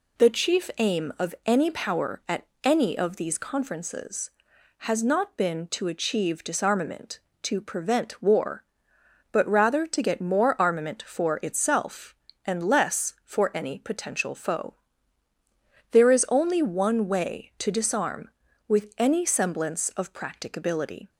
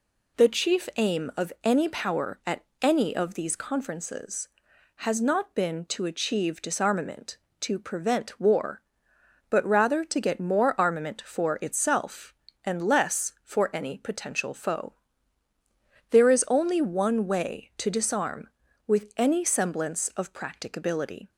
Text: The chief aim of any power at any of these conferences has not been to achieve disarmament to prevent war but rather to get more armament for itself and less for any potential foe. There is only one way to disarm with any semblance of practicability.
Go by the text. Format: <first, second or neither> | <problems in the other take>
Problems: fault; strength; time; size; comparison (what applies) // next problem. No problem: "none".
neither | pauses between "at" and "any"; slight; the same in both